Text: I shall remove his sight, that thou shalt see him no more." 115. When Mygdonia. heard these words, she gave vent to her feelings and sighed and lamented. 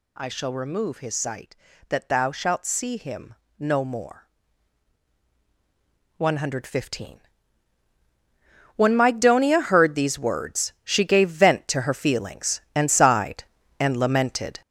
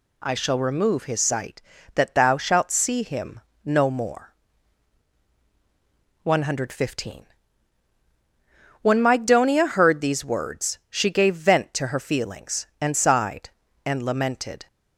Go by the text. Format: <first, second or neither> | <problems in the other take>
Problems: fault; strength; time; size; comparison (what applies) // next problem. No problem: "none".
second | gets louder; throughout; 6.5 dB // pauses between "him" and "no"; slight; at 3.3 s; 0.24 s long; slight in the second